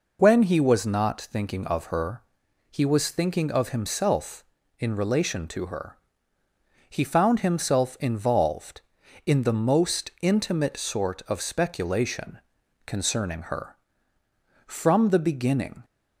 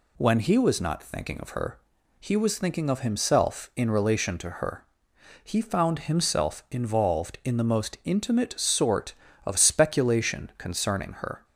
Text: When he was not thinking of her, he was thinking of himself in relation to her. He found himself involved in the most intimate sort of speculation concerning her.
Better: second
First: pauses between "speculation" and "concerning"; noticeable; at 12.3 s; 0.48 s long // goes on to say "From the beginning"; noticeable; from 14.6 s on; 1.1 s long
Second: none

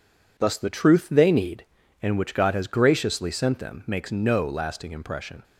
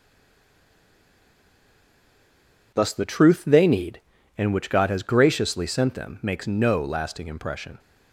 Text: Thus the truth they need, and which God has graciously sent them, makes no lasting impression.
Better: first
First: none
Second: stays silent before the first word; strong; until 2.7 s; 2.7 s long

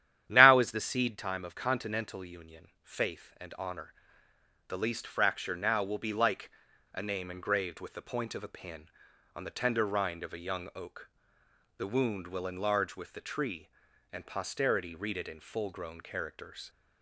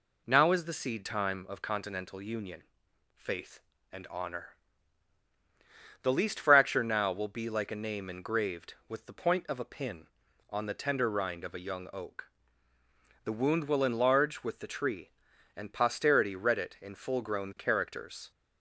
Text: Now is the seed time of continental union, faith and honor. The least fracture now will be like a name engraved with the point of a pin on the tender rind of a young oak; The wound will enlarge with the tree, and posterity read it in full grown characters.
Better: second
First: starts louder than the rest; strong; until 1.2 s; 10.5 dB // pauses between "like" and "a"; at 6.5 s; 0.43 s long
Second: none

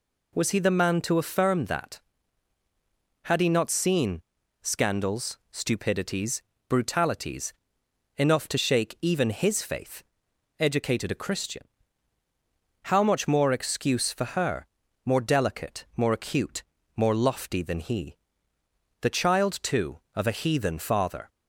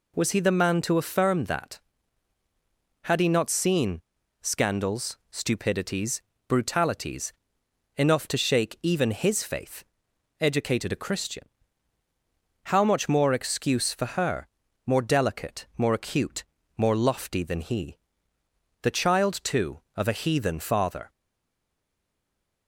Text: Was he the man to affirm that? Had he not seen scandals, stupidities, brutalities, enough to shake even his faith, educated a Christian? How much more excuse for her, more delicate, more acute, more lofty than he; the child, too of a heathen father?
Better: first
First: pauses between "seen" and "scandals"; at 4.2 s; 0.40 s long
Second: pauses between "seen" and "scandals"; at 4.0 s; 0.40 s long // stays silent after the last word; noticeable; from 21.0 s on; 1.6 s long

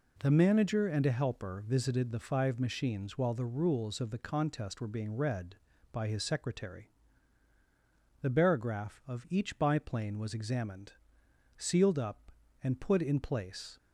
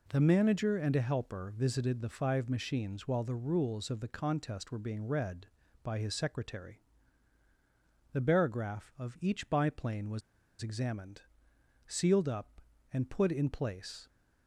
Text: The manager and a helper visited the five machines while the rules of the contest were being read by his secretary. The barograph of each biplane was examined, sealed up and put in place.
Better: first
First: none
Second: pauses between "was" and "examined"; at 10.2 s; 0.40 s long

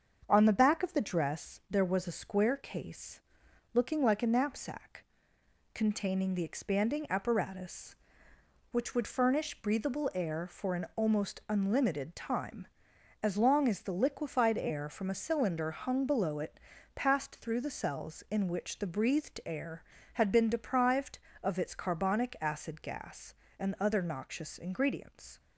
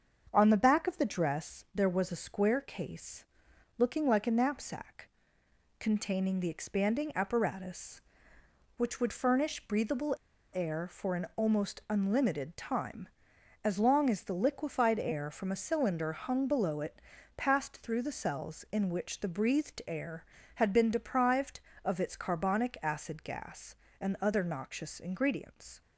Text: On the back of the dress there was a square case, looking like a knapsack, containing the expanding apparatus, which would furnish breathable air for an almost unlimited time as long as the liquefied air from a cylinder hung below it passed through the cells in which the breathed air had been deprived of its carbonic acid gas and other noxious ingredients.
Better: first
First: starts louder than the rest; until 1.3 s; 7 dB // pauses between "it" and "passed"; slight; at 16.5 s; 0.36 s long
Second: starts louder than the rest; until 1.3 s; 7 dB // pauses between "breathable" and "air"; at 10.1 s; 0.40 s long // pauses between "it" and "passed"; slight; at 17.0 s; 0.36 s long

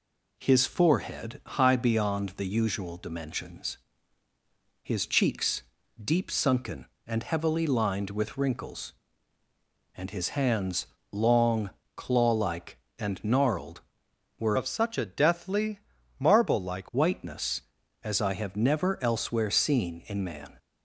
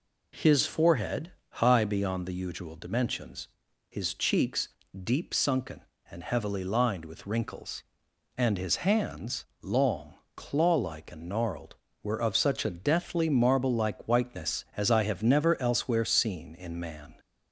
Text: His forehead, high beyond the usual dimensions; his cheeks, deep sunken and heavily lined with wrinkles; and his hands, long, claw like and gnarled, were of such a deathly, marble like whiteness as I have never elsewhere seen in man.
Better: second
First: changes voice from "of" to "like"; from 14.5 to 16.8 s; 2.3 s long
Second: none

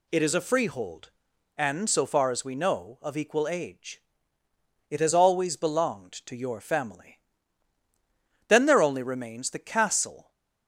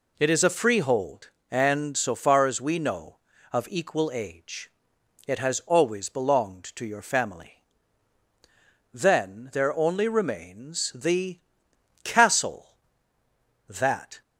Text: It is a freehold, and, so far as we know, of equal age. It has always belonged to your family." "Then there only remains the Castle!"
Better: first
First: none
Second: pauses between "the" and "Castle"; noticeable; at 11.4 s; 0.64 s long // goes on to say "That"; from 13.6 s on; 0.54 s long

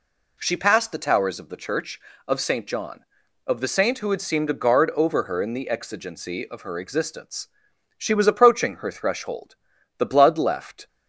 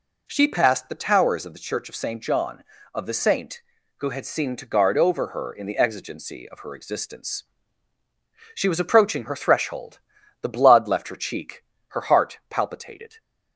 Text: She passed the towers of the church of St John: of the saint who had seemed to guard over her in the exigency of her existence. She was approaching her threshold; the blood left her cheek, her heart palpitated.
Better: second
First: stops before "her cheek her heart palpitated"; at 10.8 s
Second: none

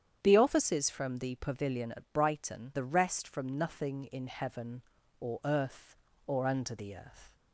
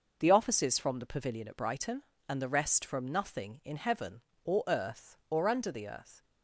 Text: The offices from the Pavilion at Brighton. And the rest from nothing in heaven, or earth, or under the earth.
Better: second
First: starts louder than the rest; strong; until 1.2 s; 9 dB // skips "And"; at 2.7 s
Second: none

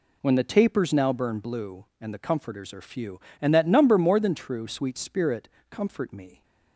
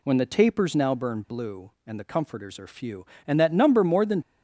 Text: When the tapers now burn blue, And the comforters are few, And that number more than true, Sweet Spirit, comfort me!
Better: first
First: none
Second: stops before "true Sweet Spirit comfort me"; at 4.2 s

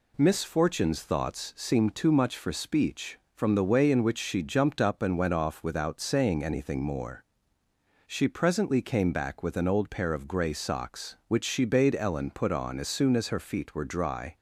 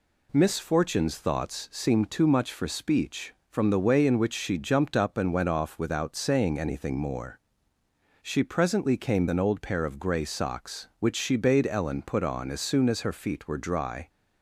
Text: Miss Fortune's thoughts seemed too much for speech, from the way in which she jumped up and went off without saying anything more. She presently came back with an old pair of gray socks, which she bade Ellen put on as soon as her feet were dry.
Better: first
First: none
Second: skips "back with"; at 9.2 s

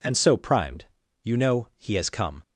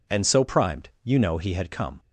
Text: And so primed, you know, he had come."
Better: second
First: says "has" for "had"; at 1.9 s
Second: none

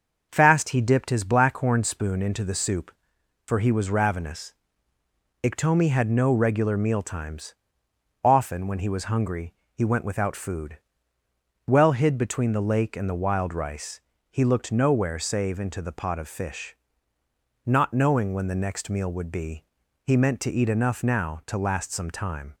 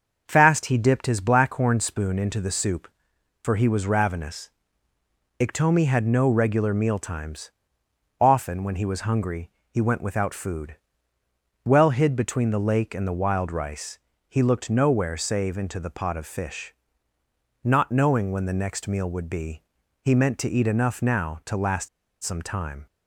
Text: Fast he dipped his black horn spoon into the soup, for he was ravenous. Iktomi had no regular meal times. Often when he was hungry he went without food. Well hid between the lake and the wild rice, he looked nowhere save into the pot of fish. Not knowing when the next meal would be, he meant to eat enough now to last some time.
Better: first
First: starts louder than the rest; until 1.3 s; 6.5 dB // pauses between "hungry" and "he"; slight; at 9.5 s; 0.20 s long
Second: starts louder than the rest; until 1.2 s; 6.5 dB // pauses between "hungry" and "he"; slight; at 9.4 s; 0.20 s long // pauses between "last" and "some"; slight; at 21.8 s; 0.35 s long

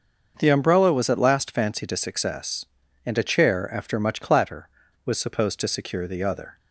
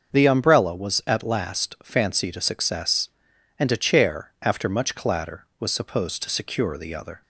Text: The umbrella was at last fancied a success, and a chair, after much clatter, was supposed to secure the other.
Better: neither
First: starts louder than the rest; until 1.4 s; 6.5 dB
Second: starts louder than the rest; until 1.1 s; 6.5 dB

